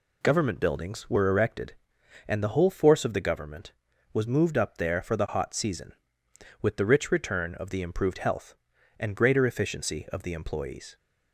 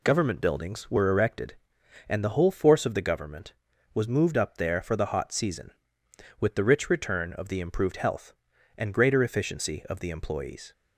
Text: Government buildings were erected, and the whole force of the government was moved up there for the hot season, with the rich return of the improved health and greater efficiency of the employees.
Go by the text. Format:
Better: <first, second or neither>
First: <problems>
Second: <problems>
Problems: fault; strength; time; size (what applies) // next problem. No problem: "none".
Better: neither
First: none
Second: none